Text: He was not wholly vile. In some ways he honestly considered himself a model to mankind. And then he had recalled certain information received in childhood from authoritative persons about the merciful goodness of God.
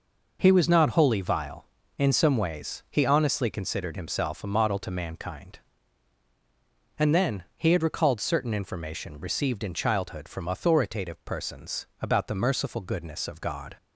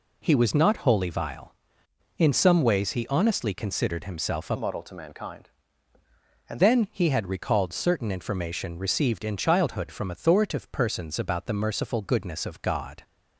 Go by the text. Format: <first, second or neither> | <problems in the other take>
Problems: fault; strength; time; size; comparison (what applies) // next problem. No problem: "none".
first | changes voice from "model" to "And"; from 4.5 to 6.6 s; 2.1 s long